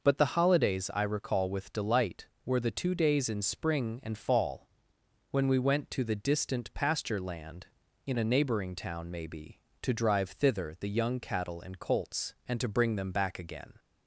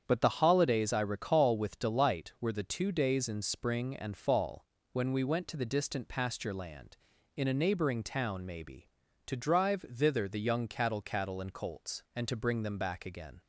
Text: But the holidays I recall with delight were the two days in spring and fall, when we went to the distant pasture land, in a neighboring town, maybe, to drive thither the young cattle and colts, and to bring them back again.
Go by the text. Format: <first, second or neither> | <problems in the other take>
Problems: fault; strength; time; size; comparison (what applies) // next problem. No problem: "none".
first | starts louder than the rest; strong; until 1.0 s; 8 dB // says "cattle" twice; at 11.0 s